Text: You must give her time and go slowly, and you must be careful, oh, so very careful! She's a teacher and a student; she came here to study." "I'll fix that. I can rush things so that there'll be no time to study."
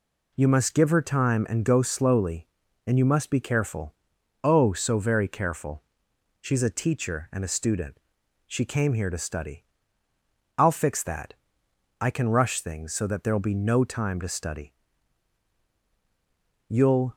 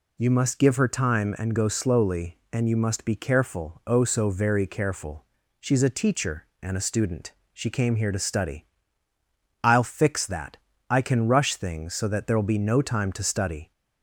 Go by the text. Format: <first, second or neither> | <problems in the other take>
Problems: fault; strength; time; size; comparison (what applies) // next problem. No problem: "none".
second | goes on to say "You'll"; slight; from 16.6 s on; 0.48 s long